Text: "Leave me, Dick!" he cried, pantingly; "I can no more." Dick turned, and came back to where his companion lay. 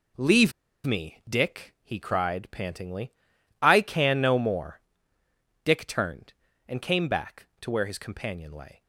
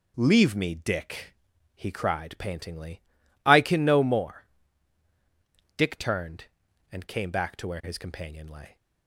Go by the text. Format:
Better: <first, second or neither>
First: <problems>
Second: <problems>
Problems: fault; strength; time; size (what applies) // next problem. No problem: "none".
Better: second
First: pauses between "Leave" and "me"; slight; at 0.5 s; 0.34 s long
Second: none